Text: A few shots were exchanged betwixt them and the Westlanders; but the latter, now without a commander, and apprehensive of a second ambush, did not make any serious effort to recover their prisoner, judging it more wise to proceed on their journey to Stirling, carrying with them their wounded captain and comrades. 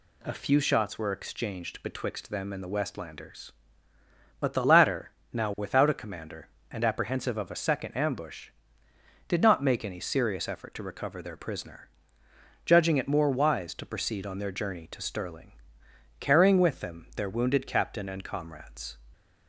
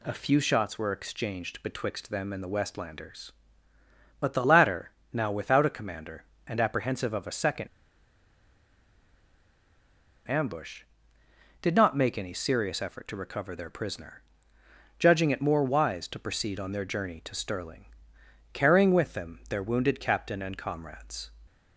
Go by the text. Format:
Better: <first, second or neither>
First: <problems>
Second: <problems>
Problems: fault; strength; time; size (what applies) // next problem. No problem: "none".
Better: first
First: none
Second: pauses between "second" and "ambush"; strong; at 7.6 s; 2.6 s long